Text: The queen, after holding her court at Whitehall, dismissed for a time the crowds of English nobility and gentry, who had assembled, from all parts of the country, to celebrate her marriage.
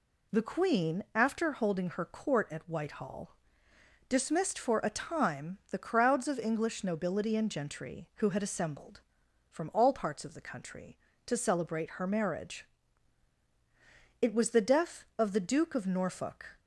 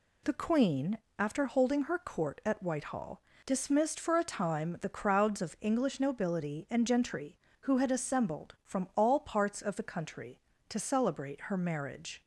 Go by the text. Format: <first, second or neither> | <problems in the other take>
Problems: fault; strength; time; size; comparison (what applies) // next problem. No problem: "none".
second | goes on to say "It was the death of the duke of Norfolk"; strong; from 14.2 s on; 2.3 s long